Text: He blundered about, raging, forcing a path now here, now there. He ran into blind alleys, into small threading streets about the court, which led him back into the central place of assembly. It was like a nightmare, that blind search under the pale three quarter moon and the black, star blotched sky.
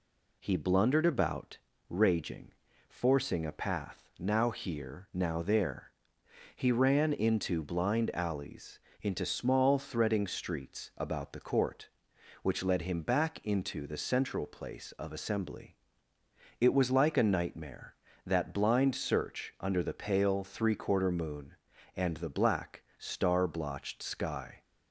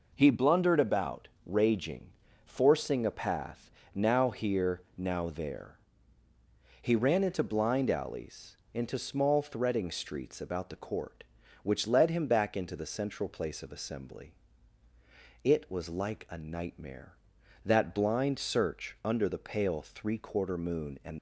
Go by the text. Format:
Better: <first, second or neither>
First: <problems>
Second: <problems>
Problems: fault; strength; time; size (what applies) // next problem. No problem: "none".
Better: first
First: none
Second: pauses between "path" and "now"; slight; at 3.7 s; 0.24 s long // stops before "the black star blotched sky"; at 21.1 s